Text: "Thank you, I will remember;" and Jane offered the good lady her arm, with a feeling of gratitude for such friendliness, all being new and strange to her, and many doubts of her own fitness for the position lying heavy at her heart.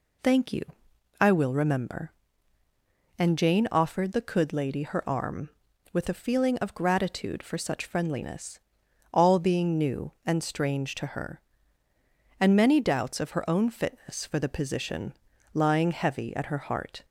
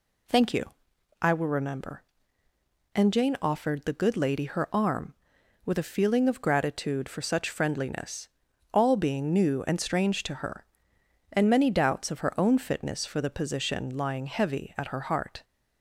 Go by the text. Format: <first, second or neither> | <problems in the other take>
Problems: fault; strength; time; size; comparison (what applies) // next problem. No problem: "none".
second | says "could" for "good"; at 4.2 s // pauses between "position" and "lying"; at 15.1 s; 0.40 s long